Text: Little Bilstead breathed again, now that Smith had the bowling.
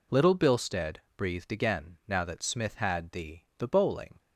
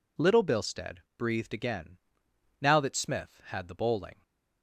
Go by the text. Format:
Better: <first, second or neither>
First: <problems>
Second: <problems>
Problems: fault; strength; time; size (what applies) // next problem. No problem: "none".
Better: second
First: pauses between "Bilstead" and "breathed"; slight; at 0.9 s; 0.22 s long // says "the" twice; at 3.5 s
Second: pauses between "Bilstead" and "breathed"; slight; at 1.0 s; 0.16 s long